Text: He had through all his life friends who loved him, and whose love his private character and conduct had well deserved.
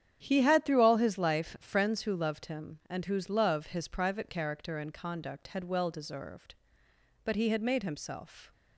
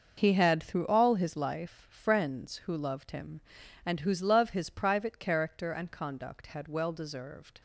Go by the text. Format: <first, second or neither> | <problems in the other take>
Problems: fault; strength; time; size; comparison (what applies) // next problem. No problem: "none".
second | starts louder than the rest; strong; until 1.2 s; 9 dB; noticeable in the second // goes on to say "But he had made himself"; noticeable; from 7.2 s on; 1.2 s long